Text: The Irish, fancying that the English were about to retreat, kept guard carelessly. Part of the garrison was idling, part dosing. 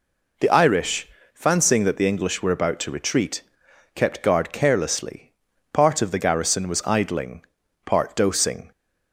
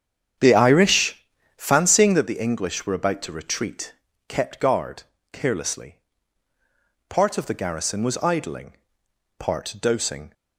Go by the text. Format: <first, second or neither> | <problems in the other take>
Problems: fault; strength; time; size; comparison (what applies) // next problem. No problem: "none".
first | starts louder than the rest; strong; until 2.1 s; 8 dB // pauses between "guard" and "carelessly"; slight; at 5.0 s; 0.28 s long